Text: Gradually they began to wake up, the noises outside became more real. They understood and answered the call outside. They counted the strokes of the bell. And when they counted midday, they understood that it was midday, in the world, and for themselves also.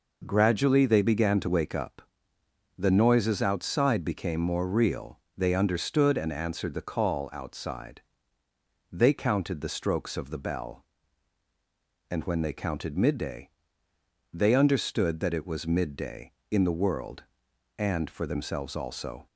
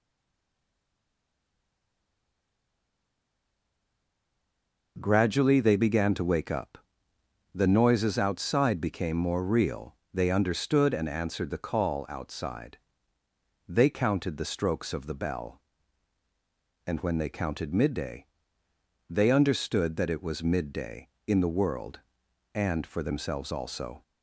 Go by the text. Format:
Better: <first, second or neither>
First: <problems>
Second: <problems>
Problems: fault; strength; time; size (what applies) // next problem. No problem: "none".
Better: first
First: none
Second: stays silent before the first word; strong; until 4.9 s; 4.9 s long